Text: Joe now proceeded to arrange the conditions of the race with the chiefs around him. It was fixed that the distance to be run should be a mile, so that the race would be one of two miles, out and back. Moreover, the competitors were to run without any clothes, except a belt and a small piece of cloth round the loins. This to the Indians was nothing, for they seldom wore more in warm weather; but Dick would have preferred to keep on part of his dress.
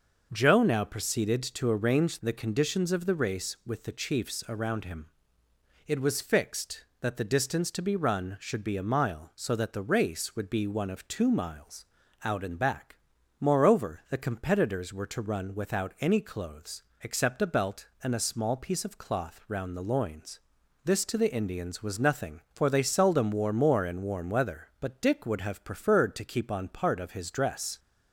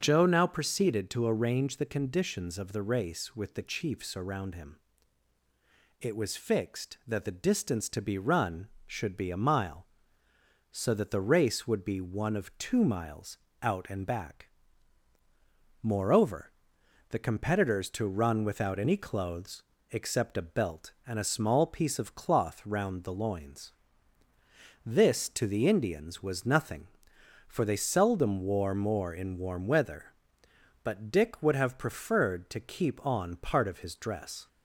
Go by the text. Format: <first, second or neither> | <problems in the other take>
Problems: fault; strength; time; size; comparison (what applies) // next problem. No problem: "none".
first | starts louder than the rest; until 1.0 s; 6.5 dB // skips "were"; at 17.8 s